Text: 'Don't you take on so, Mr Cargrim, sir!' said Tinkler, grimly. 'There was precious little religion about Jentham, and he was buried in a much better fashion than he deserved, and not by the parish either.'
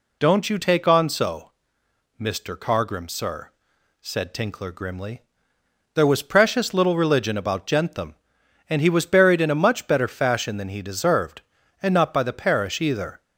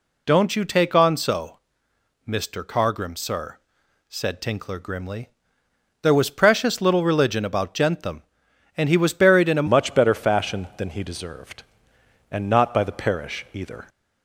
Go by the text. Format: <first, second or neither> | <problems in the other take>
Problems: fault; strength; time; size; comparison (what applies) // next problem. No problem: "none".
first | changes voice at "much"; from 9.6 s on; 4.2 s long